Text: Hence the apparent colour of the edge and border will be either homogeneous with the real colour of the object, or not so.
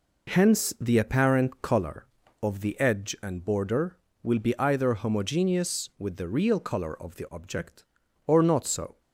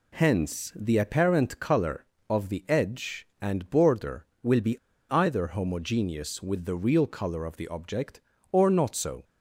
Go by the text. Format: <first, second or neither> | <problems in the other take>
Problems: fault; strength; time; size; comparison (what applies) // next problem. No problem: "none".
first | pauses between "be" and "either"; slight; at 4.7 s; 0.32 s long